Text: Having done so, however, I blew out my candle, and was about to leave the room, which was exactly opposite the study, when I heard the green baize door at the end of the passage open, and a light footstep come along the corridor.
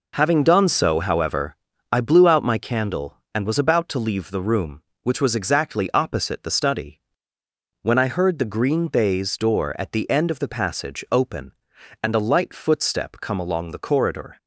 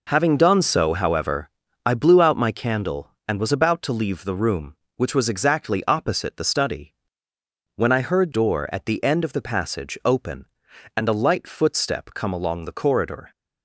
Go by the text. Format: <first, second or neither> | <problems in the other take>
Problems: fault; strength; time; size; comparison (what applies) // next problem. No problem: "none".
first | skips "the green baize"; at 8.3 s